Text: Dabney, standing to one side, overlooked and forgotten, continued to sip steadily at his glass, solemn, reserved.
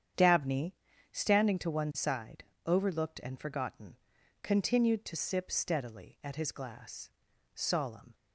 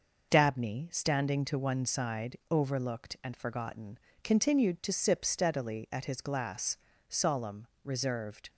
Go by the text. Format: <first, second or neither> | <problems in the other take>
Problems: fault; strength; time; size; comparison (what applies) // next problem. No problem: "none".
second | starts louder than the rest; strong; until 1.5 s; 8.5 dB // stops before "reserved"; at 8.1 s